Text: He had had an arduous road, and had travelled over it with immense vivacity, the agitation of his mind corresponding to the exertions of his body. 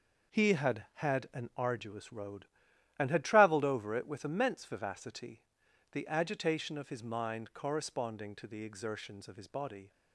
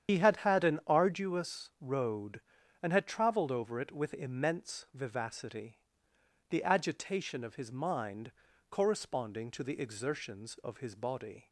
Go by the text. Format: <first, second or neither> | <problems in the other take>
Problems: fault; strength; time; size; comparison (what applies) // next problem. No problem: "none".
first | loses the start of "He"; at 0.0 s; 100 ms // starts louder than the rest; strong; until 1.1 s; 9 dB // pauses between "mind" and "corresponding"; at 8.3 s; 0.38 s long